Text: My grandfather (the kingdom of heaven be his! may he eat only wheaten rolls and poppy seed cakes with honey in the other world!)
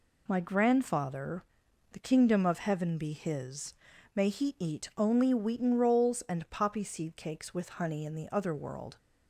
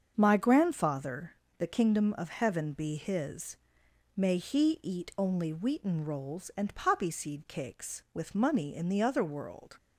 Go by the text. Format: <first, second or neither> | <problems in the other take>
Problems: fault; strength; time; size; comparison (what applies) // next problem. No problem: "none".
first | starts louder than the rest; until 1.1 s; 7 dB // says "money" for "honey"; at 8.3 s